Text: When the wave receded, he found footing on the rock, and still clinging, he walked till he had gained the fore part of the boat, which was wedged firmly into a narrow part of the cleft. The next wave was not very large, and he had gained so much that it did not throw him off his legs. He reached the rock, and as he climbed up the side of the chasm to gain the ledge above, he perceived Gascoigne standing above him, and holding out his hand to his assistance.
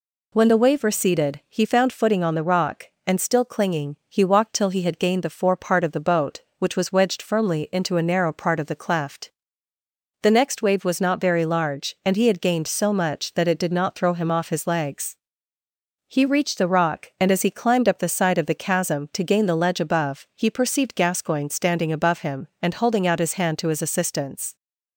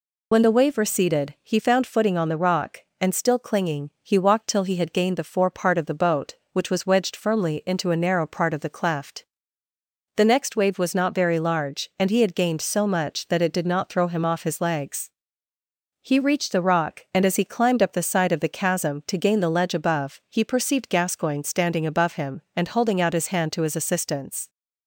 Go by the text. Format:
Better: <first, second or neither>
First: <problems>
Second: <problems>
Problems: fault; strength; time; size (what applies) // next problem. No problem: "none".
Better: first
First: none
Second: loses the start of "When"; at 0.3 s; 40 ms